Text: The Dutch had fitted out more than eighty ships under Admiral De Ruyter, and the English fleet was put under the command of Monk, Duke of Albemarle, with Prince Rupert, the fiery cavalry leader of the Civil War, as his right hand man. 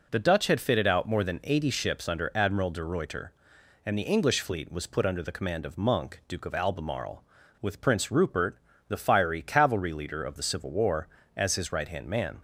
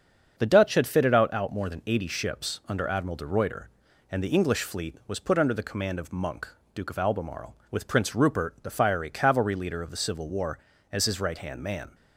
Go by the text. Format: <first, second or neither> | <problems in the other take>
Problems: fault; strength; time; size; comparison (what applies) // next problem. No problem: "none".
first | starts louder than the rest; until 1.3 s; 6.5 dB // says "out" twice; at 1.3 s